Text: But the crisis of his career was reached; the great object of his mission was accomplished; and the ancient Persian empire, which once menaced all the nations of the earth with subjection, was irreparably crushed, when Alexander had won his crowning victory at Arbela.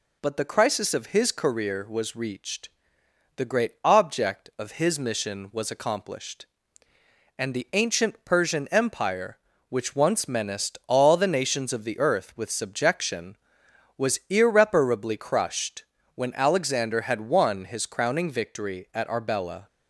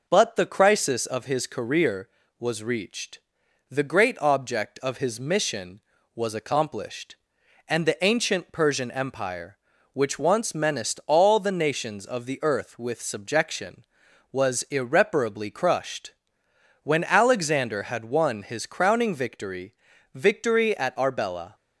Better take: first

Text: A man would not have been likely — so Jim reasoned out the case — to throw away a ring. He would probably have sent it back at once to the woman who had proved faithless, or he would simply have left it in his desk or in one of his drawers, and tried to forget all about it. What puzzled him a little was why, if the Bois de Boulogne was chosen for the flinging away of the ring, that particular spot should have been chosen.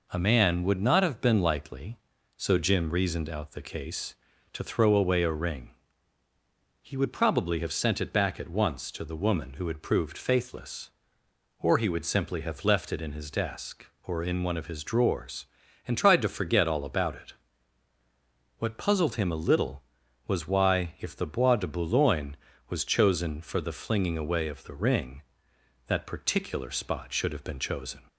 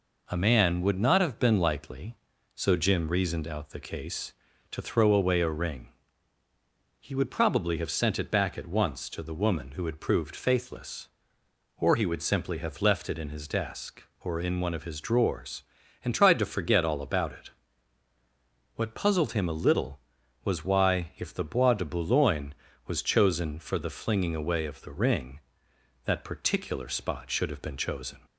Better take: neither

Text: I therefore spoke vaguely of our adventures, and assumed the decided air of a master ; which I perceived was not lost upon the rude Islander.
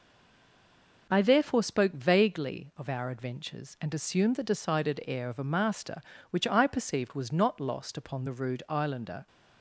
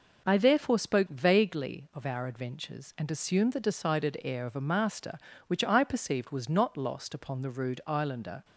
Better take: second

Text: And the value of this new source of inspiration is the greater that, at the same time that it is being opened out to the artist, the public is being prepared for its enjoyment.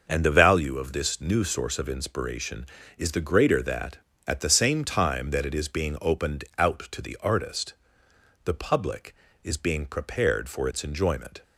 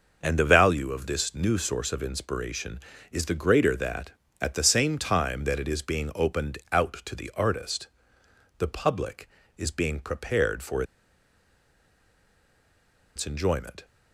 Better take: first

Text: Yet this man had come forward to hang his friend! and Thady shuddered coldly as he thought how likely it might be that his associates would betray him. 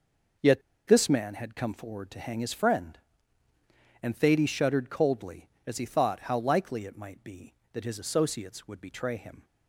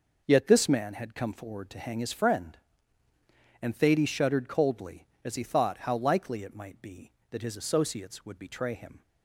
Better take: second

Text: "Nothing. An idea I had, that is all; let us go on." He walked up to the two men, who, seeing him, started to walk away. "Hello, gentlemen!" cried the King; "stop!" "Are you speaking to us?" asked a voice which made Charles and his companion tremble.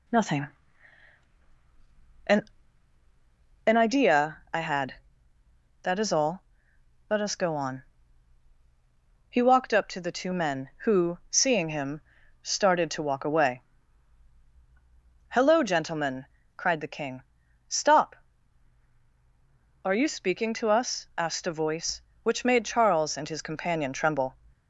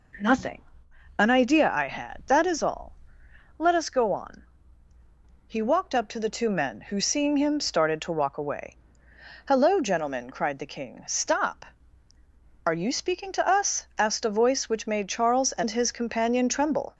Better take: second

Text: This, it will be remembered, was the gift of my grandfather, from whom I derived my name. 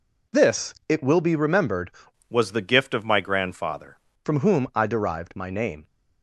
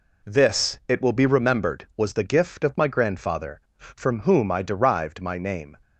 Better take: second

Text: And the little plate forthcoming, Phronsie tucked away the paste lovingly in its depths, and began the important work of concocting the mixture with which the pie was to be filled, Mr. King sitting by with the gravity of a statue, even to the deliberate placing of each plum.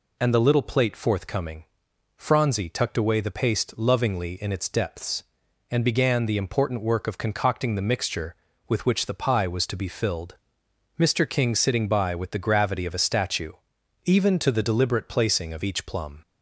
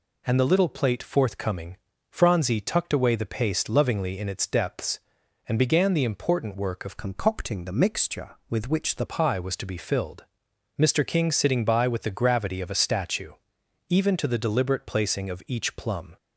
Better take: first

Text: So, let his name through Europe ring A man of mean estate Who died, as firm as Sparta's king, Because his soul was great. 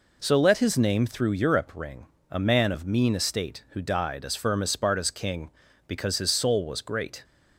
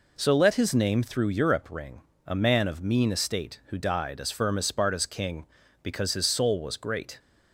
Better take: neither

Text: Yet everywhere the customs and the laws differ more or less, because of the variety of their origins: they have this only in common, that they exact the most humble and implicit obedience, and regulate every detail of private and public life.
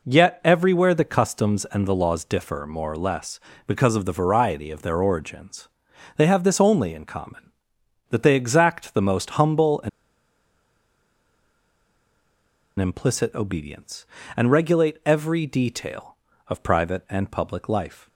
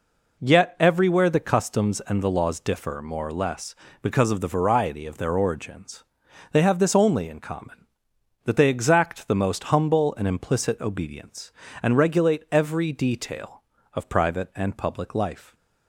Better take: second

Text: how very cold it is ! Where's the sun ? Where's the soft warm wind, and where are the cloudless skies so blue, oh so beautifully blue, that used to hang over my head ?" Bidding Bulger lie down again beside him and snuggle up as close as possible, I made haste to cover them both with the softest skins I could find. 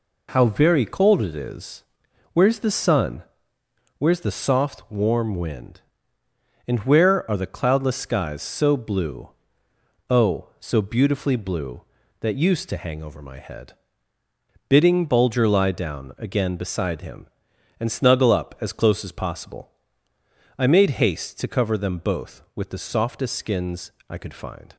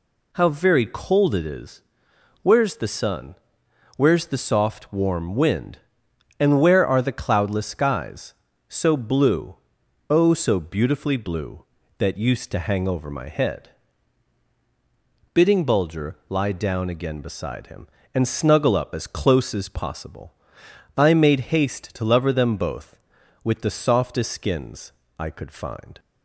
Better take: first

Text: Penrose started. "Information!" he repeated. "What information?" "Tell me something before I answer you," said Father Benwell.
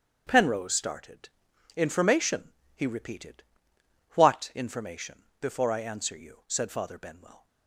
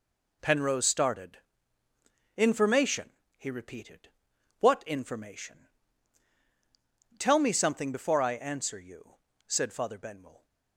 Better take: second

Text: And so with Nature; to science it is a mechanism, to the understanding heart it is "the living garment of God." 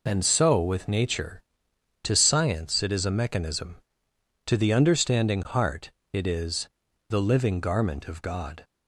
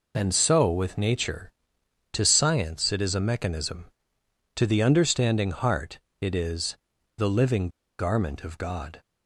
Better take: first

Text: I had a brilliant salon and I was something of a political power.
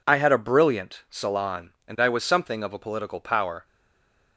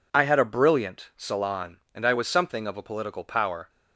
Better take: second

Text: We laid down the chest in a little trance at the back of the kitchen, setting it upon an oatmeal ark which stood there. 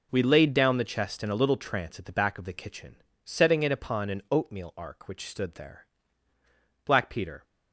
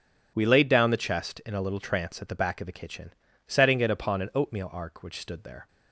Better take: second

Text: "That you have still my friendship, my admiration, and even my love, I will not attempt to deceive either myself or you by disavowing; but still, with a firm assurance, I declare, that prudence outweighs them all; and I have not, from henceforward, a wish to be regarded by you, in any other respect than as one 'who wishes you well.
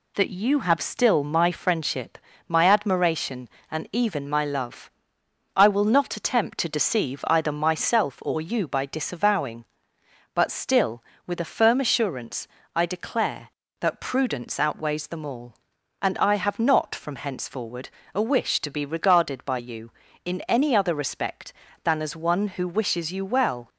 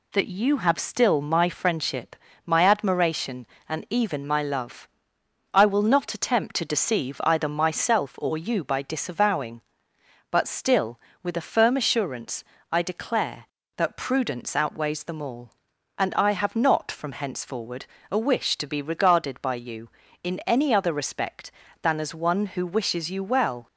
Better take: neither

